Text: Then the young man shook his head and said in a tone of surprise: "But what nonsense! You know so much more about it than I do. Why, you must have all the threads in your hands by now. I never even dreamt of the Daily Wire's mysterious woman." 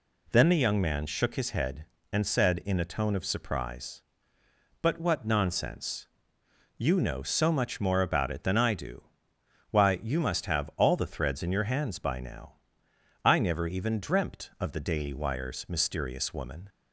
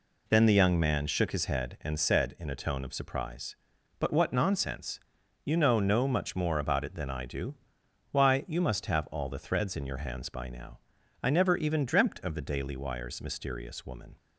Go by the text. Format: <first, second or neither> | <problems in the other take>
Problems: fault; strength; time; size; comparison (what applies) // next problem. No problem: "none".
first | says "no" for "so"; at 5.7 s